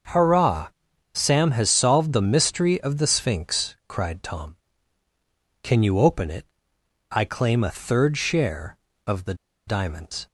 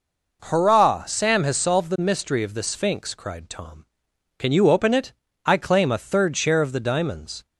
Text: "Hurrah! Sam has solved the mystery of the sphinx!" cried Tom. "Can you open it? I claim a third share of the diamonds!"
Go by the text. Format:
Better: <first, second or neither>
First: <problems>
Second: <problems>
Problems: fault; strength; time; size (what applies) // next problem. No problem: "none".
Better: second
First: starts louder than the rest; noticeable; until 1.5 s; 6 dB // pauses between "the" and "diamonds"; slight; at 9.3 s; 0.33 s long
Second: none